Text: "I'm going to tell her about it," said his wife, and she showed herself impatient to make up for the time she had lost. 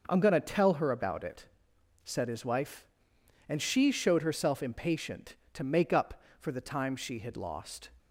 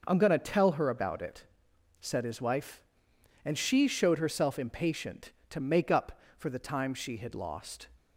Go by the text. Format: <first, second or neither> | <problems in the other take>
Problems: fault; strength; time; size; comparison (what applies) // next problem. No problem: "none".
neither | starts louder than the rest; noticeable; the same in both